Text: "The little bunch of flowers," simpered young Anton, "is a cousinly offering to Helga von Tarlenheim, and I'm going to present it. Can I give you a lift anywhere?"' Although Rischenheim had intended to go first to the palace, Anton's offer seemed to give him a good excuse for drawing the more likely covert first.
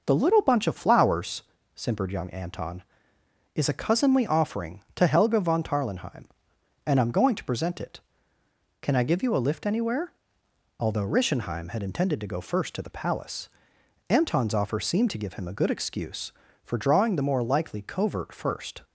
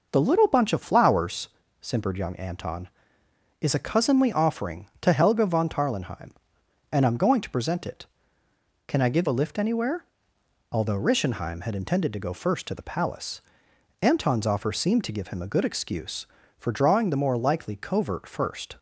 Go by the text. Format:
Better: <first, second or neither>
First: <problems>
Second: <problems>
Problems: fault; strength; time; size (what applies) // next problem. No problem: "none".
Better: first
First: none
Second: skips "you"; at 9.2 s